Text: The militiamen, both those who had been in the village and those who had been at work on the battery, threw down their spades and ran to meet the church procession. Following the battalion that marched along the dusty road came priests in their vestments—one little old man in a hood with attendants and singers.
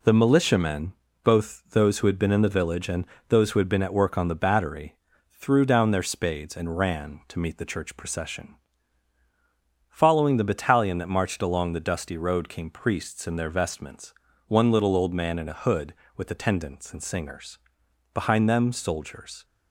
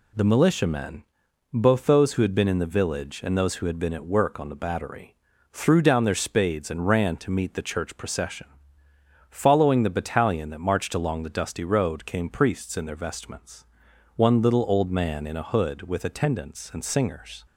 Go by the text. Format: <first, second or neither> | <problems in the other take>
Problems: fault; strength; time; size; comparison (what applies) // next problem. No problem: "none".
second | pauses between "and" and "those"; slight; at 3.0 s; 0.24 s long // goes on to say "Behind them soldiers"; noticeable; from 18.1 s on; 1.3 s long